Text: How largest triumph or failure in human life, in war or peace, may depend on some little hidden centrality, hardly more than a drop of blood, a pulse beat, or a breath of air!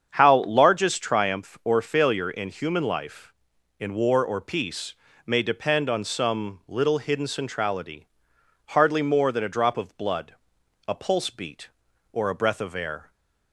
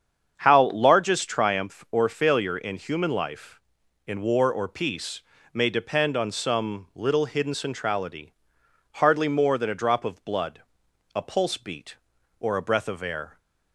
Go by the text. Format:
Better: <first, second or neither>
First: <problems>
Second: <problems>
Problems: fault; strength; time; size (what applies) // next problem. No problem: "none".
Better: neither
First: starts louder than the rest; strong; until 1.1 s; 7.5 dB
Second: starts louder than the rest; strong; until 1.3 s; 7.5 dB